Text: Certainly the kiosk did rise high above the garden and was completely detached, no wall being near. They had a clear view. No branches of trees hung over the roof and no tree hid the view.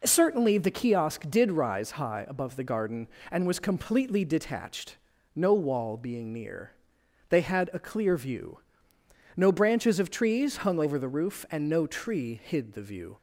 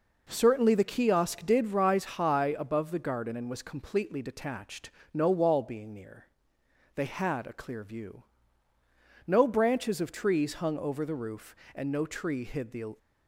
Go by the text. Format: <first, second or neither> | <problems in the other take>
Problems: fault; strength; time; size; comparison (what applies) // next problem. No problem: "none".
first | stops before "view"; at 12.9 s